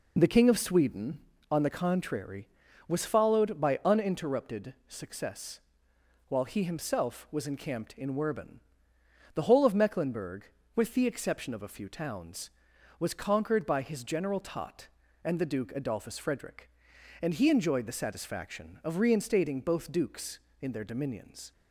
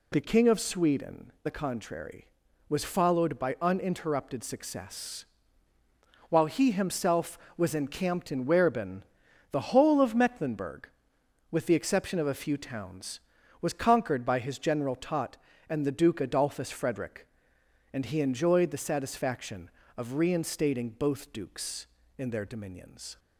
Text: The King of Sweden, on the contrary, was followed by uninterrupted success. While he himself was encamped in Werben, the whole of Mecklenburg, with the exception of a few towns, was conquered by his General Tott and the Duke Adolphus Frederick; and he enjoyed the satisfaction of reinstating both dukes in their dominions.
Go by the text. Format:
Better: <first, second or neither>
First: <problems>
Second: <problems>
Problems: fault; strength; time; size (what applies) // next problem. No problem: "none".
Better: first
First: none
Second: skips "on"; at 1.3 s